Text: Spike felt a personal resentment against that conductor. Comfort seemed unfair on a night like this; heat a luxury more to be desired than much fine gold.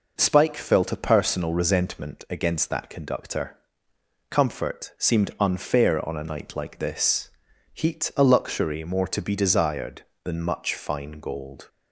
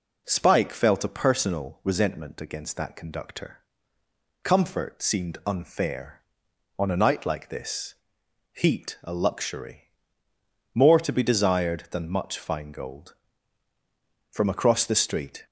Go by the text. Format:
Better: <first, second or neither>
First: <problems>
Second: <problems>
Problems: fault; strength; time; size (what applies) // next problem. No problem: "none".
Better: first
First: none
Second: pauses between "luxury" and "more"; noticeable; at 9.8 s; 0.90 s long // goes on to say "From across the street"; noticeable; from 14.3 s on; 1.1 s long